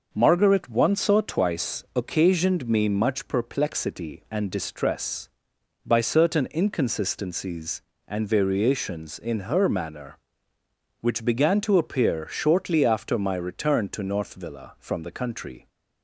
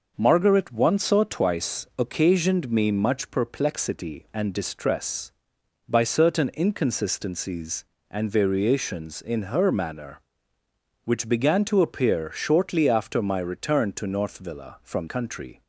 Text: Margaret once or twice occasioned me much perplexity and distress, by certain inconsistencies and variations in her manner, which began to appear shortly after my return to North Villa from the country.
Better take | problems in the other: first | skips "the"; at 15.0 s

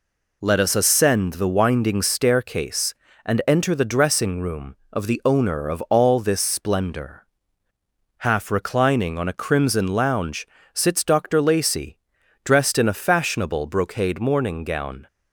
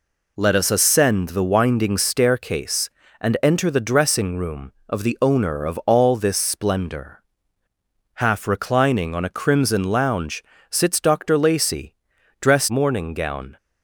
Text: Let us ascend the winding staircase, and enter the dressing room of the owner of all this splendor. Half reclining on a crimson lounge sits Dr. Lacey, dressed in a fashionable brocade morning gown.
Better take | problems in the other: first | pauses between "lounge" and "sits"; slight; at 10.4 s; 0.28 s long; slight in the first // skips "in a fashionable brocade"; at 12.6 s

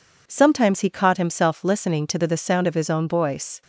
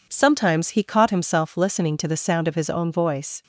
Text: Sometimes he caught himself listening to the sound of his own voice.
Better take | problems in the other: second | says "the" twice; at 2.2 s

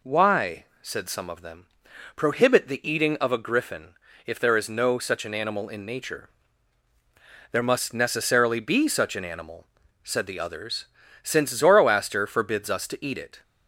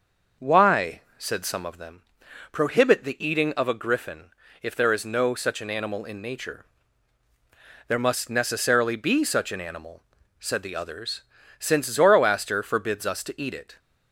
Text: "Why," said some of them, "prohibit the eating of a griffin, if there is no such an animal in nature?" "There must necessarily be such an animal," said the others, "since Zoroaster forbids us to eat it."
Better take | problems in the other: first | starts louder than the rest; noticeable; until 1.9 s; 6 dB

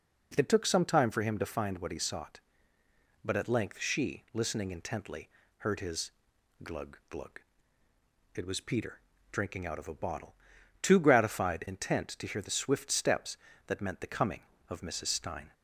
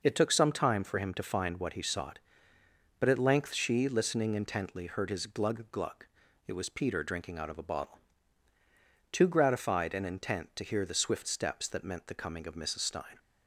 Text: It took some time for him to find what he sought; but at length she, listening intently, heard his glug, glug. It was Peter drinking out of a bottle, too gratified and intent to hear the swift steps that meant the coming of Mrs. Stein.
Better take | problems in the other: second | pauses between "his" and "glug"; noticeable; at 6.1 s; 0.52 s long // pauses between "Peter" and "drinking"; slight; at 9.0 s; 0.30 s long // skips "and"; at 11.6 s

